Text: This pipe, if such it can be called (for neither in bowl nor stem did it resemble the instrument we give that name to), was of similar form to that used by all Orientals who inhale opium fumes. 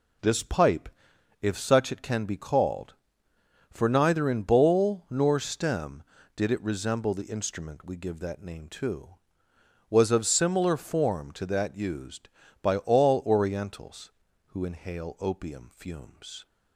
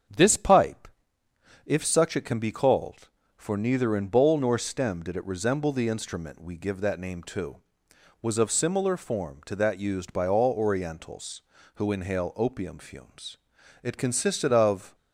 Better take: first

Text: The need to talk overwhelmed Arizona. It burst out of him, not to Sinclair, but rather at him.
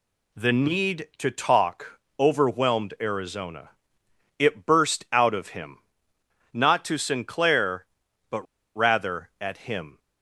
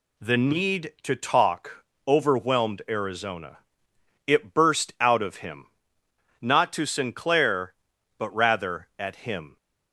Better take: second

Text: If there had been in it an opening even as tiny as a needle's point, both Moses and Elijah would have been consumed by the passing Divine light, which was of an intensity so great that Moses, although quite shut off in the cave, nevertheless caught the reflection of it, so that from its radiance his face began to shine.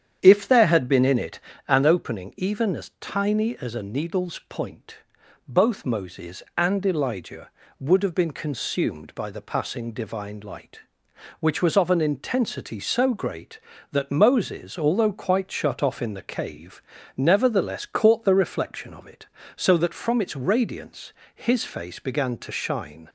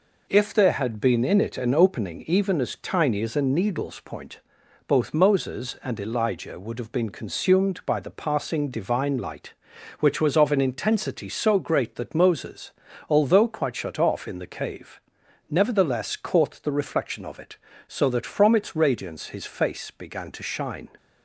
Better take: second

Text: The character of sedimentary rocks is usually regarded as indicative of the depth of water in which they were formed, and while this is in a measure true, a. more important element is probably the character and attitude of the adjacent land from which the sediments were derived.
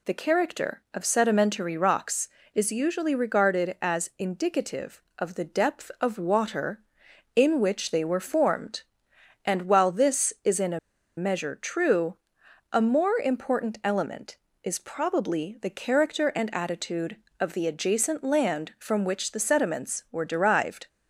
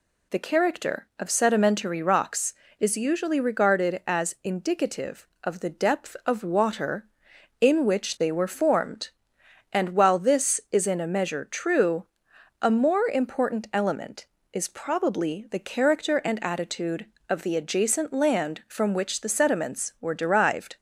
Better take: second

